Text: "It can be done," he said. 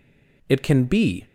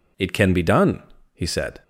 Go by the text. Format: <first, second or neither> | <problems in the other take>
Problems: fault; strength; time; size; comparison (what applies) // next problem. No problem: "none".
second | stops before "done he said"; at 1.2 s